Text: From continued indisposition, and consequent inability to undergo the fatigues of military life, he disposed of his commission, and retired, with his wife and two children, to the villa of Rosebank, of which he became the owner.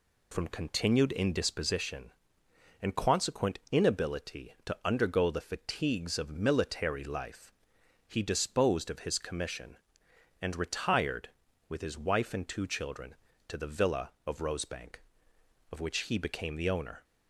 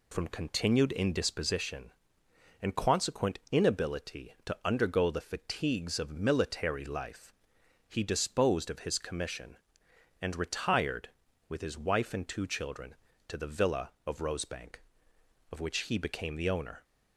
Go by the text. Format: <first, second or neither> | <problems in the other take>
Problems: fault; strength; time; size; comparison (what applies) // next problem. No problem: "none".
neither | none